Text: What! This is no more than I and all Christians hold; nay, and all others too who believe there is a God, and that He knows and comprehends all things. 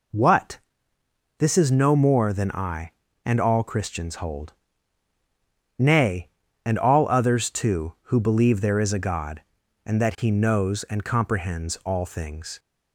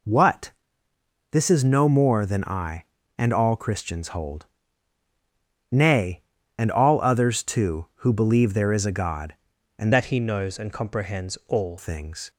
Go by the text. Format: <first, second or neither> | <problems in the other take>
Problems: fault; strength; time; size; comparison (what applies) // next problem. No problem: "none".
first | changes voice from "that" to "all"; from 9.9 to 11.7 s; 1.8 s long